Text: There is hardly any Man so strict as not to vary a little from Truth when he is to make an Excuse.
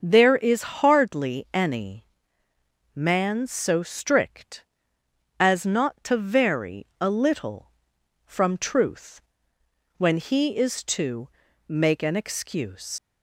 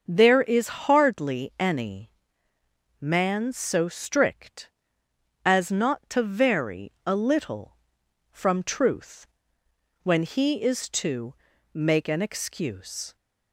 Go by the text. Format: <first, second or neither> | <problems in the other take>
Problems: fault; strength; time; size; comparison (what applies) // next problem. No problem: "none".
second | starts louder than the rest; until 1.0 s; 6.5 dB; also in the second // pauses between "any" and "Man"; noticeable; at 2.0 s; 0.90 s long; noticeable in the second // pauses between "Truth" and "when"; noticeable; at 9.2 s; 0.76 s long; noticeable in the second // pauses between "to" and "make"; at 11.2 s; 0.40 s long; also in the second // leaves "Excuse" unfinished; at 12.9 s; 110 ms